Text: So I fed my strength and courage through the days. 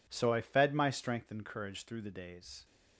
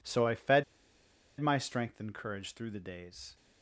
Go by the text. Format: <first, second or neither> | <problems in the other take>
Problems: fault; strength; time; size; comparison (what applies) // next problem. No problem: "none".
first | pauses between "fed" and "my"; noticeable; at 0.6 s; 0.77 s long